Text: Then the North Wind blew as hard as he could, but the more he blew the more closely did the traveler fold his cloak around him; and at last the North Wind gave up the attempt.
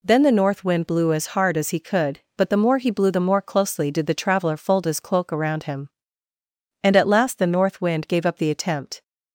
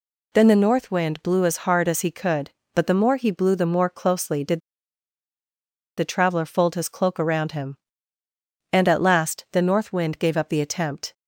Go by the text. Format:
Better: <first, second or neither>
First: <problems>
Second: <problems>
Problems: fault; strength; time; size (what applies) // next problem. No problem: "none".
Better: first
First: none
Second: pauses between "did" and "the"; strong; at 4.5 s; 1.3 s long